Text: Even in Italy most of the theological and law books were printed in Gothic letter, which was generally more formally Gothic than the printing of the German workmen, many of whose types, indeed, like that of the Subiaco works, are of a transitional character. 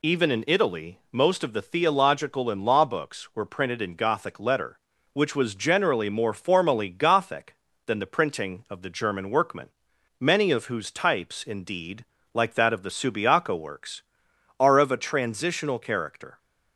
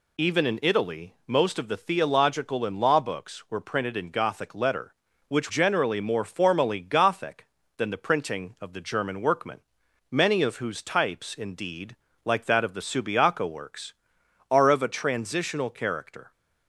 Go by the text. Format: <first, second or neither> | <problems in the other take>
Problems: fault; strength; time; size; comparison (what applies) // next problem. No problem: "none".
first | skips "was"; at 5.4 s